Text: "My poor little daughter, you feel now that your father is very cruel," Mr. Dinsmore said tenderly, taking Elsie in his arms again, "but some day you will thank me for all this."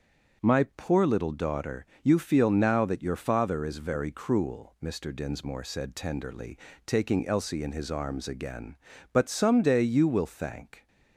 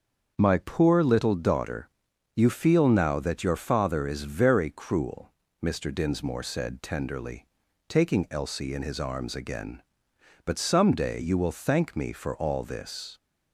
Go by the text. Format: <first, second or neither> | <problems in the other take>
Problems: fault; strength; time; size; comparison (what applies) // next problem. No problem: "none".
second | starts louder than the rest; until 1.4 s; 6.5 dB; also in the second // stops before "me for all this"; at 10.8 s